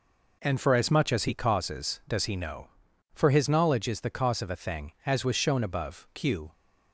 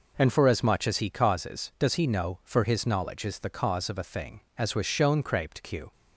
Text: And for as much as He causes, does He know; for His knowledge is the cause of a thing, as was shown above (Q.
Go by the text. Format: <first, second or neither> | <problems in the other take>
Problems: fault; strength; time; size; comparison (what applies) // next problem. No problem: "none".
first | says "craped" for "above"; at 5.2 s